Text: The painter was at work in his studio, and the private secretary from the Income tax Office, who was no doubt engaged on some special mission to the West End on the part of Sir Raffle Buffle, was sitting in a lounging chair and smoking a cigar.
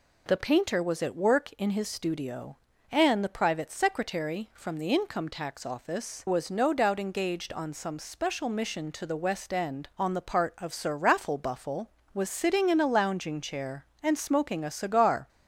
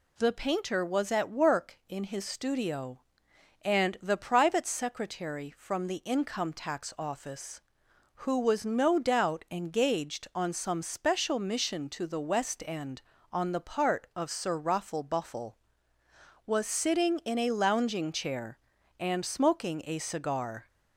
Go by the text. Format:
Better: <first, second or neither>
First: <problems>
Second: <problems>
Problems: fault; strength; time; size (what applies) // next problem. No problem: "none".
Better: second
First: skips "who"; at 6.2 s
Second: none